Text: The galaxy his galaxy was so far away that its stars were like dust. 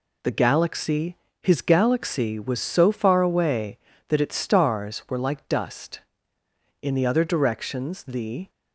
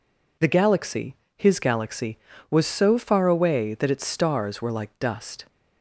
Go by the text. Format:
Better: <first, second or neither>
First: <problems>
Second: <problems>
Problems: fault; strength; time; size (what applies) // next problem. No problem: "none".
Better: second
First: pauses between "galaxy" and "his"; slight; at 1.1 s; 0.26 s long // goes on to say "In the other directions the"; strong; from 6.8 s on; 1.6 s long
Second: pauses between "galaxy" and "his"; slight; at 1.1 s; 0.22 s long